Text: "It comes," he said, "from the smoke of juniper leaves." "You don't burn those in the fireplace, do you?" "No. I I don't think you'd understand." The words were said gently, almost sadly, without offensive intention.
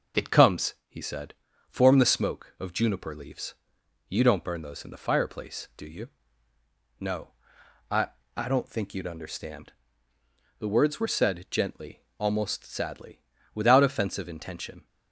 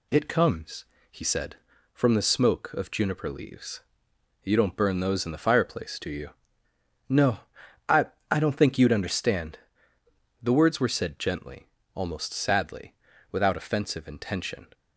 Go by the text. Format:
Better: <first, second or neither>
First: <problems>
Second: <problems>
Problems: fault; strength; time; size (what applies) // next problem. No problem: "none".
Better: second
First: says "form" for "from"; at 1.6 s // pauses between "I" and "I"; slight; at 8.0 s; 0.26 s long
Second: pauses between "I" and "I"; slight; at 8.0 s; 0.24 s long